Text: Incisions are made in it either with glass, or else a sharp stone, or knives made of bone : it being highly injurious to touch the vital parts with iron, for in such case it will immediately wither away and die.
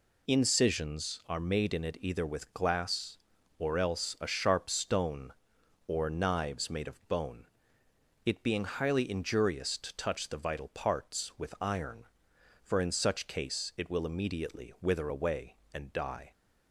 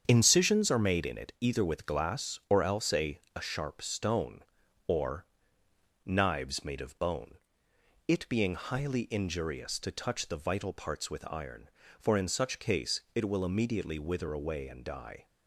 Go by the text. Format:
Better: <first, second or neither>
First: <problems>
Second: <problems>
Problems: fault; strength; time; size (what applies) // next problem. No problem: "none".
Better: first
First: none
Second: starts louder than the rest; strong; until 1.0 s; 8 dB // says "a" twice; at 3.3 s // pauses between "or" and "knives"; noticeable; at 5.2 s; 0.78 s long // pauses between "case" and "it"; slight; at 12.9 s; 0.16 s long